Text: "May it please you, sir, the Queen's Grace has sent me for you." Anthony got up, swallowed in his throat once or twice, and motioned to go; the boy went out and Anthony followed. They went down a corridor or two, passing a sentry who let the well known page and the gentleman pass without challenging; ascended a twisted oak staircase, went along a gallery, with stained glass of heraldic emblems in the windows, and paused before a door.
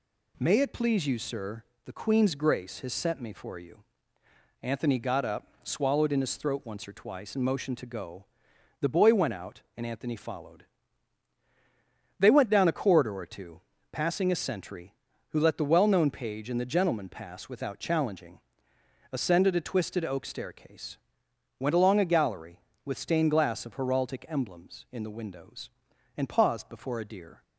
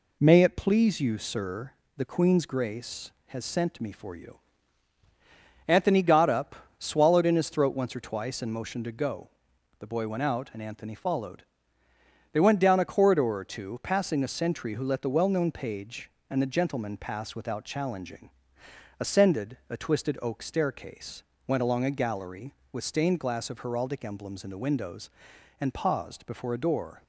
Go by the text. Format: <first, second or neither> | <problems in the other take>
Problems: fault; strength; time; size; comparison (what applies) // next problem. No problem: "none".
second | says "deer" for "door"; at 27.0 s